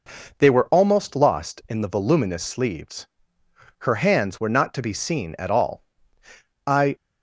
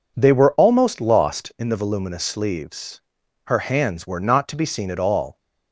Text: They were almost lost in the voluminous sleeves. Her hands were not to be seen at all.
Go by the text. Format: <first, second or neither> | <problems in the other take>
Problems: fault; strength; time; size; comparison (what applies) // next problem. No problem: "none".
second | goes on to say "I"; slight; from 6.6 s on; 0.30 s long